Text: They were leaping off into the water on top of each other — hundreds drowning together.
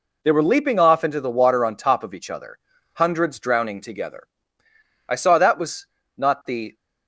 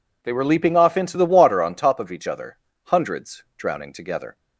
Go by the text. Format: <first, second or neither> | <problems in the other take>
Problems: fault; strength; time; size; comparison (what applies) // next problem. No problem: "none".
second | goes on to say "I saw that was not the"; strong; from 5.0 s on; 1.6 s long